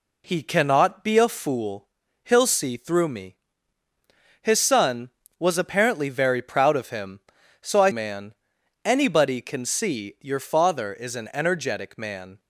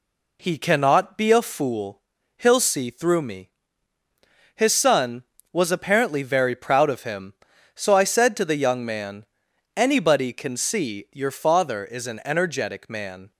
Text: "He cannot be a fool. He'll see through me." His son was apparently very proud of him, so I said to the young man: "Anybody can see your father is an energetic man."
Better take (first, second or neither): second